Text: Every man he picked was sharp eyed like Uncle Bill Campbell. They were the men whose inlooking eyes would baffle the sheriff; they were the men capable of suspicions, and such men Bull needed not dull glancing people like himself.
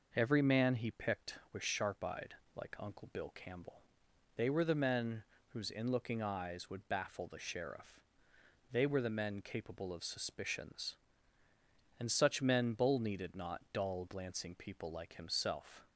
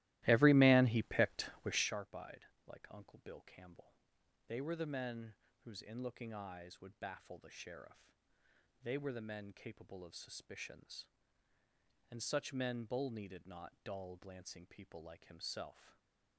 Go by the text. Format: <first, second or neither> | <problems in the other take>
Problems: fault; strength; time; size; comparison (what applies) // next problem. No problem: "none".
first | starts louder than the rest; strong; until 2.0 s; 17 dB // pauses between "eyed" and "like"; slight; at 2.4 s; 0.20 s long; slight in the first // pauses between "men" and "whose"; slight; at 5.3 s; 0.32 s long; slight in the first